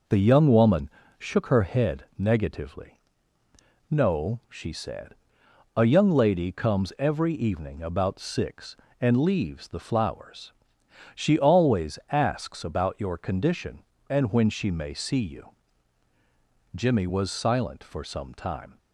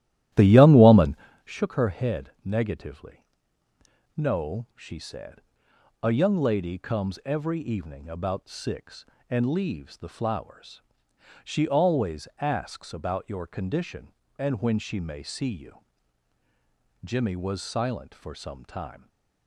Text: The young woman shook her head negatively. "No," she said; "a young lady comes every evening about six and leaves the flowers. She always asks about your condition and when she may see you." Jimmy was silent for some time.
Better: first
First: pauses between "woman" and "shook"; slight; at 0.8 s; 0.30 s long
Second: starts louder than the rest; strong; until 1.4 s; 13.5 dB // pauses between "woman" and "shook"; slight; at 1.1 s; 0.30 s long // stays silent after the last word; slight; from 18.9 s on; 0.5 s long

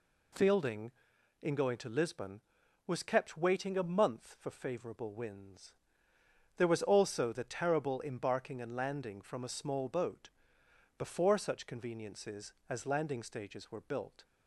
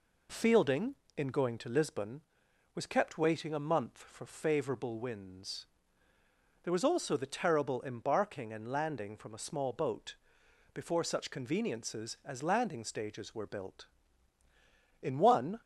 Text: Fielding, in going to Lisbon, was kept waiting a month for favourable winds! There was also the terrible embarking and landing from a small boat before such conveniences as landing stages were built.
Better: first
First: pauses between "boat" and "before"; noticeable; at 10.2 s; 0.68 s long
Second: pauses between "boat" and "before"; noticeable; at 10.1 s; 0.58 s long // goes on to say "In one"; from 15.0 s on; 0.58 s long

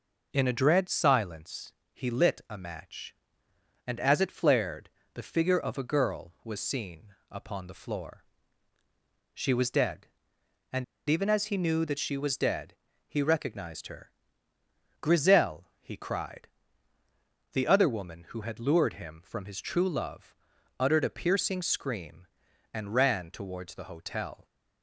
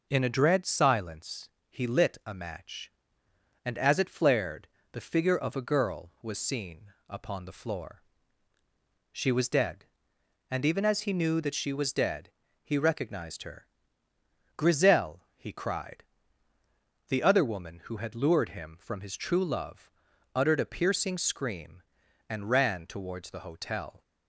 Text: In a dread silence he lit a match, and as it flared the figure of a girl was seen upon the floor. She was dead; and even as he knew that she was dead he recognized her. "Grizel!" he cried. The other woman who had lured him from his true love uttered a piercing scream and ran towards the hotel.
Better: second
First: pauses between "silence" and "he"; slight; at 1.7 s; 0.18 s long // pauses between "flared" and "the"; slight; at 4.8 s; 0.26 s long // pauses between "seen" and "upon"; slight; at 7.1 s; 0.16 s long // pauses between "and" and "even"; slight; at 10.8 s; 0.25 s long // pauses between "dead" and "he"; slight; at 12.7 s; 0.32 s long // pauses between "love" and "uttered"; at 20.3 s; 0.42 s long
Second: pauses between "silence" and "he"; slight; at 1.4 s; 0.18 s long // pauses between "flared" and "the"; slight; at 4.6 s; 0.26 s long // pauses between "seen" and "upon"; slight; at 6.9 s; 0.16 s long // pauses between "dead" and "he"; slight; at 12.3 s; 0.32 s long // pauses between "love" and "uttered"; at 19.9 s; 0.42 s long

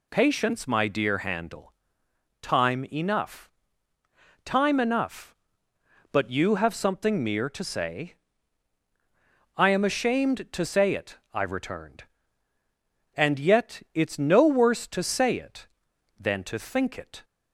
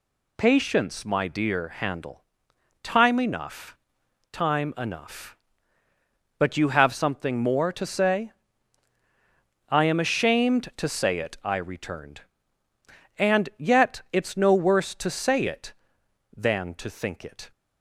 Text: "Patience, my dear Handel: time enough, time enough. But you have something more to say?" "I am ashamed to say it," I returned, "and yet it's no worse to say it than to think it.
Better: second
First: says "mere" for "more"; at 7.2 s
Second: none

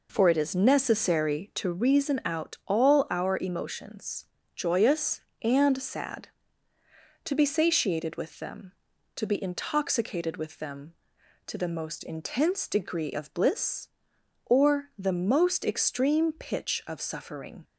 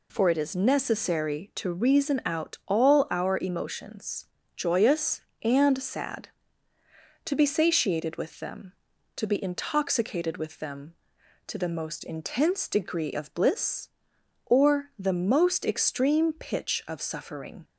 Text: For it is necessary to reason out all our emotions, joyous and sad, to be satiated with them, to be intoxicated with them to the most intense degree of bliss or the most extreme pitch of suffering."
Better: second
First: starts louder than the rest; noticeable; until 1.8 s; 4.5 dB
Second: none

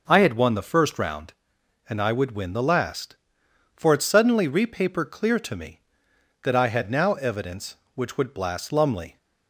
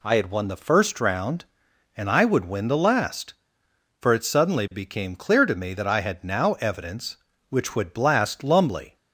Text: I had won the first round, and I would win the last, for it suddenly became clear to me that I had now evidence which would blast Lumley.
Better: second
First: says "repaper" for "became"; at 4.4 s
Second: none

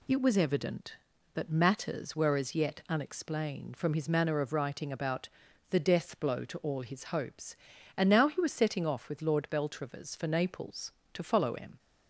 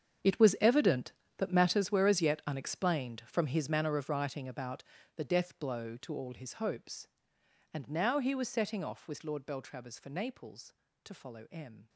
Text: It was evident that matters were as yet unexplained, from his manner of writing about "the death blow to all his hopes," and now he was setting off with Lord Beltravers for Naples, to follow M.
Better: first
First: pauses between "about" and "the"; at 5.2 s; 0.42 s long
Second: gets quieter; strong; throughout; 15.5 dB // pauses between "about" and "the"; slight; at 4.8 s; 0.32 s long

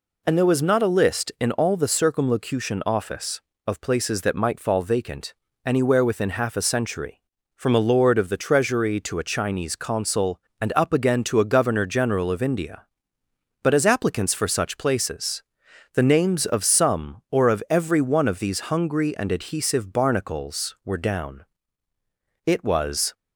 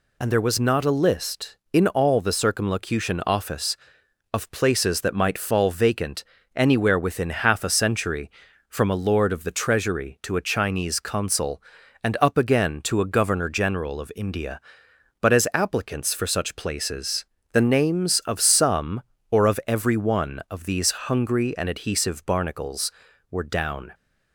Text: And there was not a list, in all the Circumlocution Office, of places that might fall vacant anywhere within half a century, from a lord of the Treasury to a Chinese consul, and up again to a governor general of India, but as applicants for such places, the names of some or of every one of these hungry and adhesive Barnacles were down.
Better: second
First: pauses between "vacant" and "anywhere"; slight; at 5.3 s; 0.32 s long // goes on to say "It was"; noticeable; from 22.4 s on; 0.68 s long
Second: pauses between "vacant" and "anywhere"; slight; at 6.2 s; 0.32 s long

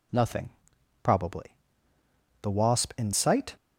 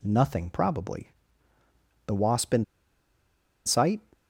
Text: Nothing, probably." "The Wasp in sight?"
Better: first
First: none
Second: pauses between "in" and "sight"; at 2.6 s; 1.0 s long

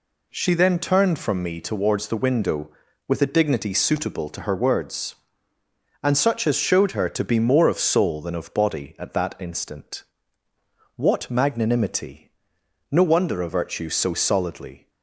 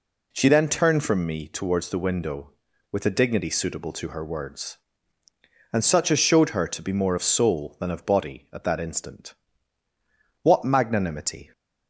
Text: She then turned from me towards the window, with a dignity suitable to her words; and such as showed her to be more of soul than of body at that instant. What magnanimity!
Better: second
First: goes on to say "No wonder a virtue so solidly"; strong; from 12.9 s on; 1.9 s long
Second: none

